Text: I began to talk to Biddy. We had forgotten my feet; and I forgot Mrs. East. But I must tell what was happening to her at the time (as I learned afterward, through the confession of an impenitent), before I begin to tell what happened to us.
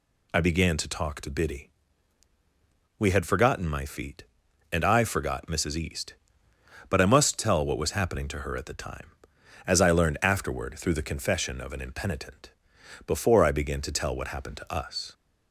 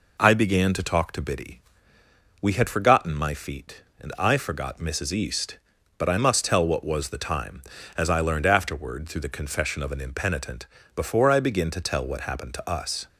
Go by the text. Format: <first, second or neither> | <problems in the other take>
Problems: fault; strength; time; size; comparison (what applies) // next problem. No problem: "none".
first | skips "happening to her at"; at 7.0 s